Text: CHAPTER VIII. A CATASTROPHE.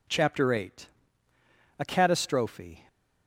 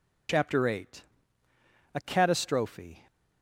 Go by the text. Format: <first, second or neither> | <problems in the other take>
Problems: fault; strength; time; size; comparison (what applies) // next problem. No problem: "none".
first | loses the start of "CHAPTER"; at 0.2 s; 65 ms